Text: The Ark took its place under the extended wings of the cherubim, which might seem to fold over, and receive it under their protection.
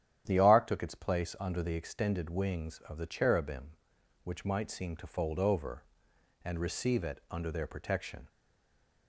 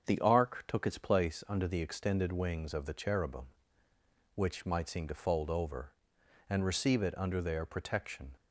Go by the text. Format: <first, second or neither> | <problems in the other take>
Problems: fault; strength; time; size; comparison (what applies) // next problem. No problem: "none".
second | starts louder than the rest; strong; until 1.2 s; 10 dB; also in the second // stays silent after the last word; slight; from 8.2 s on; 0.8 s long